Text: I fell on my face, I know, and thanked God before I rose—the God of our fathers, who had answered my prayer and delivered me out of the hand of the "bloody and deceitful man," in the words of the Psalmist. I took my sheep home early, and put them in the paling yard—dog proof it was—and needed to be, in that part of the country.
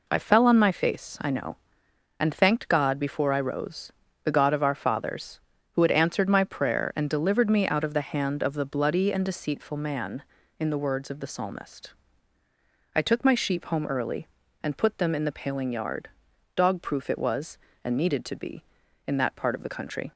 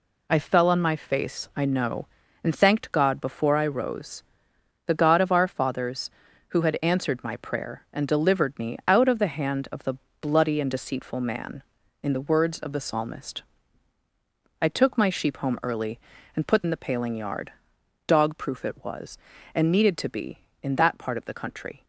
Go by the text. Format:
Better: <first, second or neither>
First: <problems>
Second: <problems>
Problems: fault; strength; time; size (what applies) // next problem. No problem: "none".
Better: first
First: none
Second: pauses between "the" and "bloody"; slight; at 9.9 s; 0.26 s long // skips "them"; at 16.6 s